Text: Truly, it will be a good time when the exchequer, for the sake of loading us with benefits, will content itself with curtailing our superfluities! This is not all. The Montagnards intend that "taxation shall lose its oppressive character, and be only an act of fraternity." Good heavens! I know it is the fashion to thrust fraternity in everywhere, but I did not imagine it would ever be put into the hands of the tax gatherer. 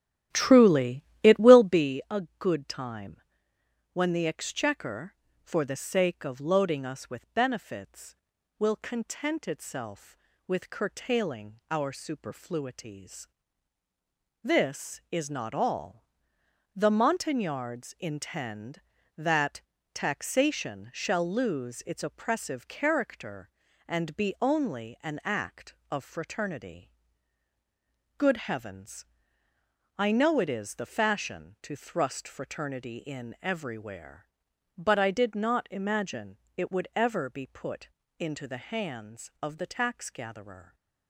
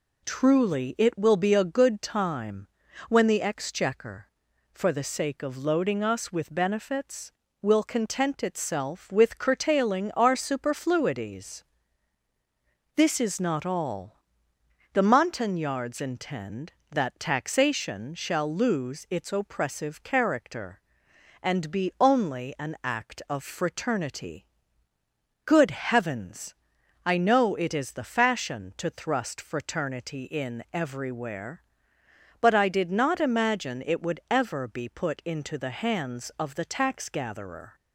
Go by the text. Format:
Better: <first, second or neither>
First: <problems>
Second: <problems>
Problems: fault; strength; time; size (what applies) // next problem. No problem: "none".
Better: second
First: starts louder than the rest; strong; until 1.9 s; 12 dB // pauses between "a" and "good"; slight; at 2.2 s; 0.16 s long // pauses between "time" and "when"; noticeable; at 3.2 s; 0.72 s long // pauses between "that" and "taxation"; slight; at 19.6 s; 0.32 s long // pauses between "imagine" and "it"; slight; at 36.3 s; 0.18 s long // pauses between "put" and "into"; slight; at 37.8 s; 0.30 s long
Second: pauses between "time" and "when"; at 2.6 s; 0.42 s long